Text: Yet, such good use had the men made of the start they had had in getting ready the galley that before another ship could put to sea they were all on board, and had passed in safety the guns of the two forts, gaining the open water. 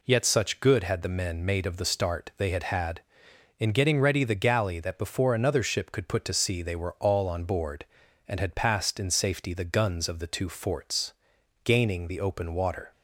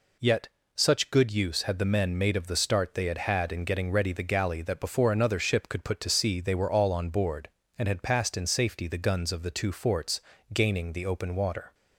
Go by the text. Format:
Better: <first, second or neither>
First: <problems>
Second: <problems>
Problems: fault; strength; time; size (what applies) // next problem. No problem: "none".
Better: second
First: skips "use"; at 0.8 s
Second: none